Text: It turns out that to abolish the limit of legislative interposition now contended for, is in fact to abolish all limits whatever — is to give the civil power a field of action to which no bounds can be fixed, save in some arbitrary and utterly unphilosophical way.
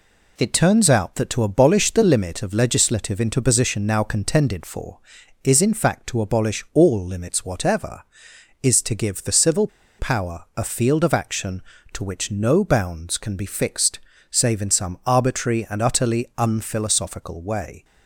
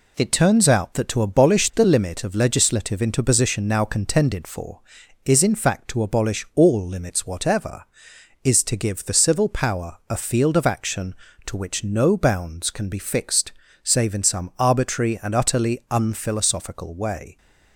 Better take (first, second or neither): second